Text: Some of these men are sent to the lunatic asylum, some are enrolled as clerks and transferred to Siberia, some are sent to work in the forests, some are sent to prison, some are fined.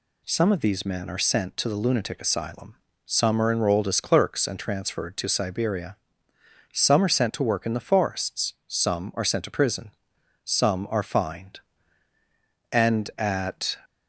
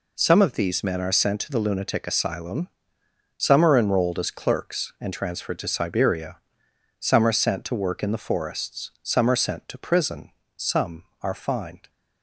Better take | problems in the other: second | goes on to say "And at"; noticeable; from 12.7 s on; 1.0 s long

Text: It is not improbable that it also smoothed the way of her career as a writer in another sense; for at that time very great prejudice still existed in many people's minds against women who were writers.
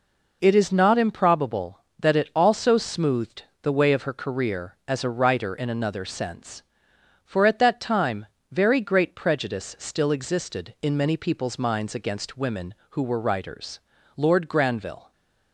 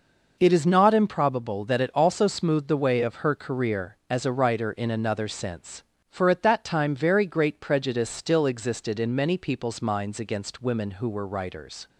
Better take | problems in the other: second | pauses between "smoothed" and "the"; slight; at 3.4 s; 0.18 s long // pauses between "time" and "very"; slight; at 8.2 s; 0.24 s long // goes on to say "Lord Granville"; noticeable; from 14.1 s on; 0.96 s long

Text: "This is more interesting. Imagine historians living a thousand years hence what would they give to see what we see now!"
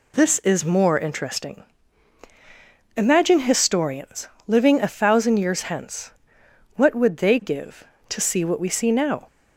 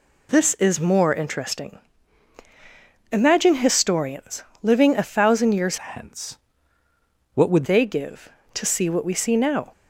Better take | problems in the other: first | pauses between "historians" and "living"; slight; at 4.4 s; 0.18 s long; slight in the first // changes voice from "hence" to "would"; from 5.7 to 7.6 s; 1.9 s long // pauses between "hence" and "what"; noticeable; at 6.3 s; 0.96 s long; noticeable in the first

